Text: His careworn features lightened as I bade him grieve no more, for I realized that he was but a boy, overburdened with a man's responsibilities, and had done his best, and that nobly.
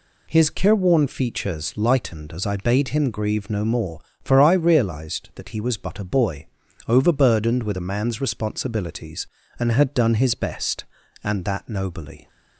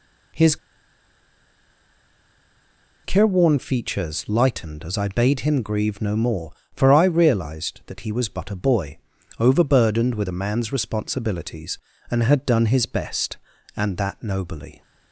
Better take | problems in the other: first | pauses between "His" and "careworn"; strong; at 0.5 s; 2.4 s long

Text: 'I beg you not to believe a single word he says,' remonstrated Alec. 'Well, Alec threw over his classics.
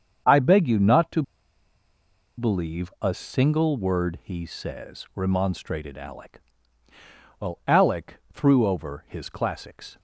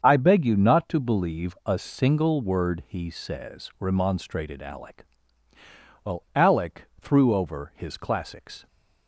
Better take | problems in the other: second | starts louder than the rest; strong; until 2.4 s; 7 dB; strong in the second // pauses between "to" and "believe"; at 1.2 s; 1.1 s long // pauses between "Alec" and "threw"; slight; at 8.1 s; 0.16 s long; slight in the second

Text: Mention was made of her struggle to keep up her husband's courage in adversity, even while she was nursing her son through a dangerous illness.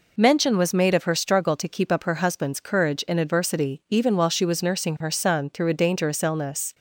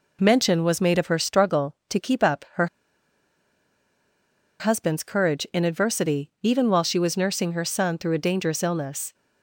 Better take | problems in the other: first | pauses between "her" and "husband's"; strong; at 2.6 s; 1.9 s long

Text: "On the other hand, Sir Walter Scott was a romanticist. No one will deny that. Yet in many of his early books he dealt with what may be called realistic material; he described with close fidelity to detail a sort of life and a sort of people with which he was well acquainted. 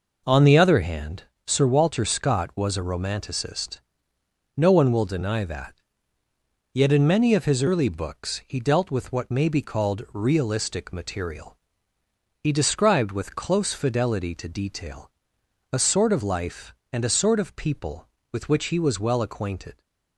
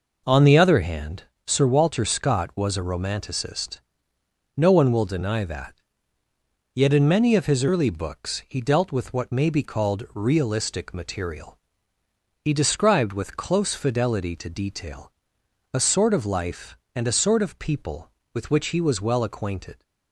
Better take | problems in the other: neither | pauses between "detail" and "a"; noticeable; the same in both

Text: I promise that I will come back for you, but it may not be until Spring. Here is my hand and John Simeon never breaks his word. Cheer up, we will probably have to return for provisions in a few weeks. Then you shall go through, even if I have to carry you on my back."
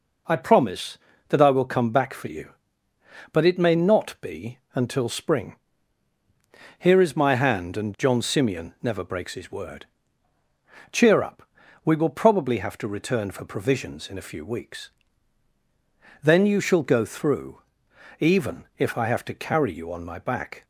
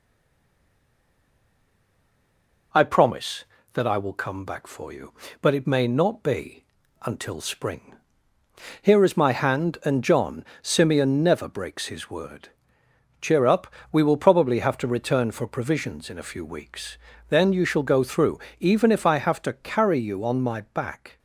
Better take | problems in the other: first | stays silent before the first word; strong; until 2.7 s; 2.7 s long // pauses between "be" and "until"; at 6.6 s; 0.40 s long; slight in the first // pauses between "John" and "Simeon"; slight; at 10.4 s; 0.18 s long

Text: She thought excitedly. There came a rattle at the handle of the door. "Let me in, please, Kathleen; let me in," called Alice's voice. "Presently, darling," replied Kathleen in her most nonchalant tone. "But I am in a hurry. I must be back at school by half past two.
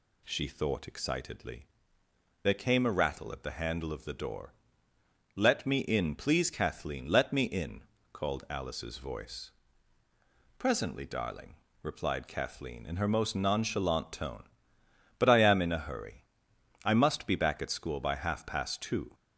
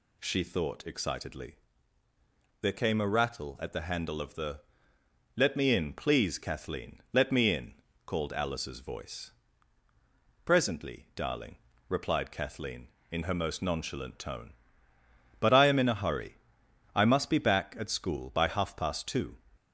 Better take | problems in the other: first | skips "door"; at 4.9 s

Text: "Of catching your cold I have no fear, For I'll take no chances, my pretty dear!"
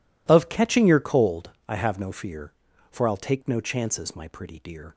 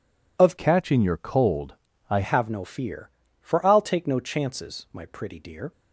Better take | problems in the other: first | changes voice from "catching" to "I"; from 0.5 to 2.1 s; 1.6 s long // pauses between "cold" and "I"; slight; at 1.7 s; 0.34 s long; slight in the first

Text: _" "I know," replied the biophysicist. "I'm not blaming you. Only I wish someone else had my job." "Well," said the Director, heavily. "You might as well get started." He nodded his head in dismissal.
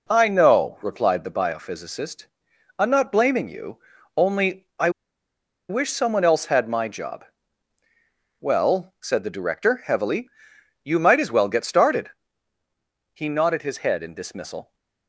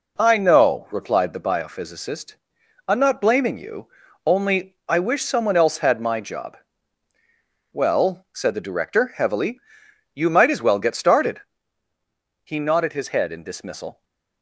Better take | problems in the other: second | pauses between "I" and "wish"; noticeable; at 4.8 s; 0.79 s long

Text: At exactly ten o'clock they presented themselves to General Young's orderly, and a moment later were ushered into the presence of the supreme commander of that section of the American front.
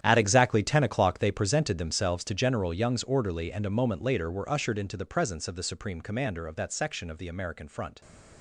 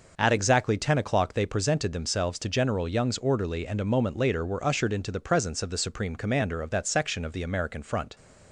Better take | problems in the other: second | gets quieter; strong; throughout; 14 dB // stays silent after the last word; slight; from 7.8 s on; 0.6 s long

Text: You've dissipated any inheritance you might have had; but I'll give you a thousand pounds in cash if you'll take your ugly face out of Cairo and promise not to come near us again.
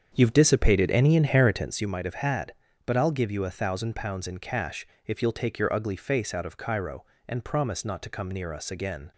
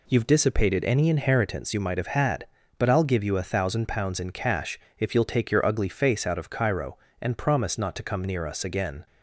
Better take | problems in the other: second | starts louder than the rest; strong; until 2.0 s; 7.5 dB // pauses between "cash" and "if"; slight; at 4.8 s; 0.22 s long; slight in the second

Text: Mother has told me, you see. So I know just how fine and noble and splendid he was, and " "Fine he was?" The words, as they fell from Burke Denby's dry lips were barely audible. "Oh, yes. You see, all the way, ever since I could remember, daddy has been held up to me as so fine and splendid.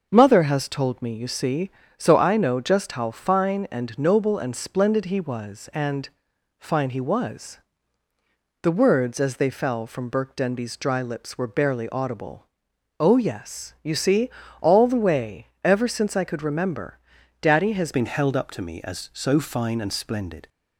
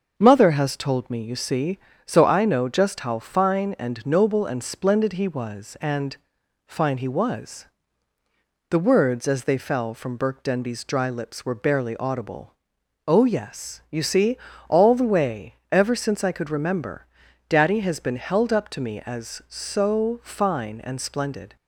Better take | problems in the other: second | starts louder than the rest; until 1.1 s; 6.5 dB; also in the second // changes voice at "been"; from 17.9 s on; 2.5 s long

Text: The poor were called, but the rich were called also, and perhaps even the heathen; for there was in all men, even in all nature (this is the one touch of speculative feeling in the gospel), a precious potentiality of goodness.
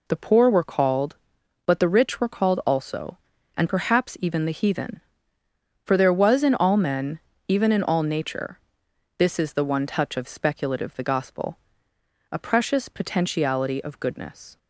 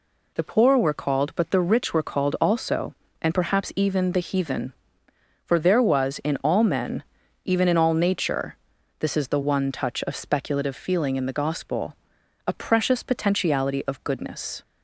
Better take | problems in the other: second | skips "feeling in"; at 10.9 s

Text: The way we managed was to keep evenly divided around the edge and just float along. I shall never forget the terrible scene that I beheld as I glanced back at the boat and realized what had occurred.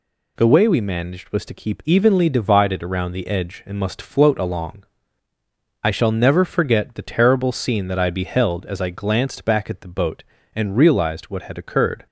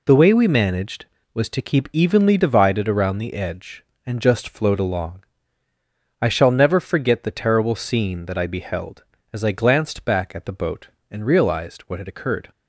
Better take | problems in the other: second | says "must" for "just"; at 3.7 s

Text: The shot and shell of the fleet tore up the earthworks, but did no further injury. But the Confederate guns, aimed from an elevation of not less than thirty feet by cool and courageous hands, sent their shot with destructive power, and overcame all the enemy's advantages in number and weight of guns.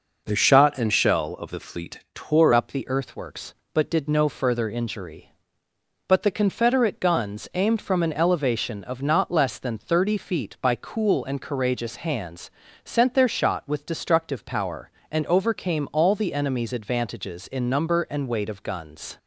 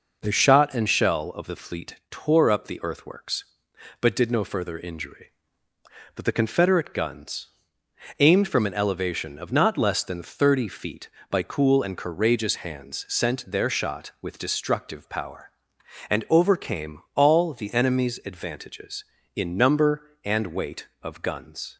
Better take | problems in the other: second | changes voice at "up"; from 2.5 s on; 16.6 s long

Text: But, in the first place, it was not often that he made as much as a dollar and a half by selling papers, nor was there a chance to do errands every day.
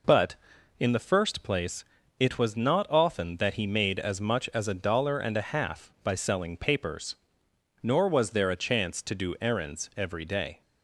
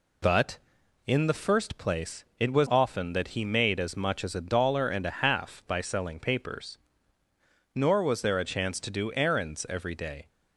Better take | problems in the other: first | skips "not"; at 2.6 s

